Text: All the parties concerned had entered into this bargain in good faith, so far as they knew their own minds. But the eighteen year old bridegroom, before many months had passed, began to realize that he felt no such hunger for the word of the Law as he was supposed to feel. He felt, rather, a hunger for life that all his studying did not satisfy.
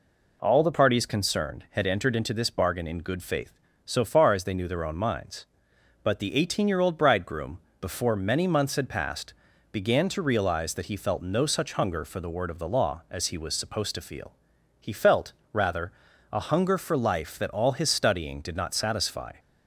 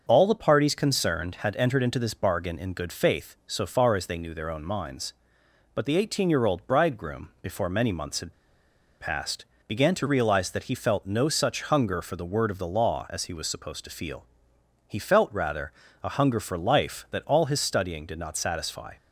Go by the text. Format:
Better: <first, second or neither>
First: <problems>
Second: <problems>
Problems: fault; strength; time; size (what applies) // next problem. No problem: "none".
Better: first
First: none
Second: starts louder than the rest; until 1.0 s; 6.5 dB // pauses between "had" and "passed"; noticeable; at 8.3 s; 0.67 s long